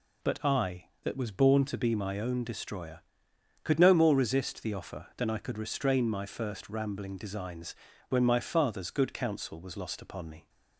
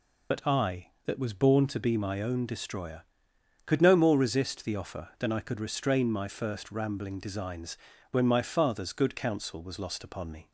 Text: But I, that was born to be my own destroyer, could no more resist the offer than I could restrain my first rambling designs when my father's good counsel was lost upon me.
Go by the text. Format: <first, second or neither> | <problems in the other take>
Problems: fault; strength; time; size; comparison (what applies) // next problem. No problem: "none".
first | loses the start of "But"; at 0.3 s; 55 ms // pauses between "designs" and "when"; slight; at 7.7 s; 0.34 s long; slight in the first